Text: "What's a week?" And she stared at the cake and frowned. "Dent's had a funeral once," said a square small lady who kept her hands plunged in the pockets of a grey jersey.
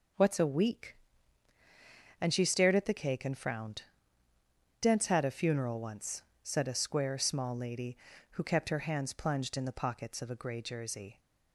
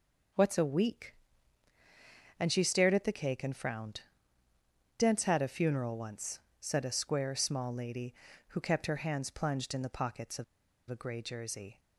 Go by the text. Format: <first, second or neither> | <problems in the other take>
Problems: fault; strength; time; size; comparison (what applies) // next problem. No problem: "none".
first | pauses between "of" and "a"; at 10.4 s; 0.44 s long